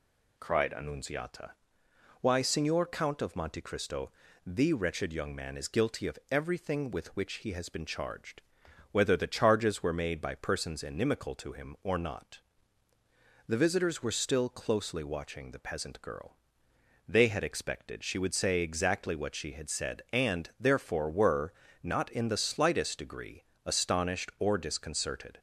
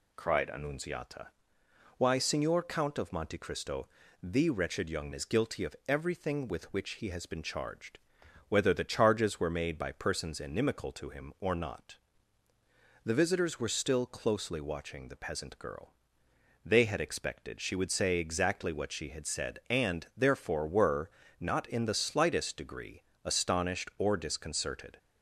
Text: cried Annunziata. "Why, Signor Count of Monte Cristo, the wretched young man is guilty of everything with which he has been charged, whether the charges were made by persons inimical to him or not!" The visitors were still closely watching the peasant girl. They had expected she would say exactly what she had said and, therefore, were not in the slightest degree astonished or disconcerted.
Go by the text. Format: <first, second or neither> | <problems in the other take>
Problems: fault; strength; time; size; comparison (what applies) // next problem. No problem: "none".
first | skips "man"; at 5.1 s // pauses between "were" and "not"; slight; at 21.0 s; 0.30 s long; slight in the first // pauses between "degree" and "astonished"; slight; at 23.0 s; 0.24 s long; slight in the first